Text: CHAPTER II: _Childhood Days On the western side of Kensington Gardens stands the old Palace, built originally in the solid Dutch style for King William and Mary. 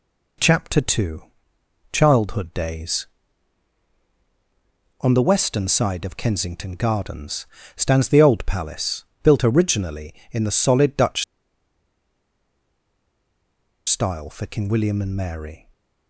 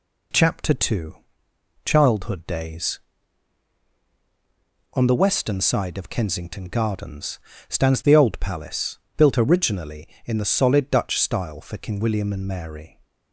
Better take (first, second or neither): second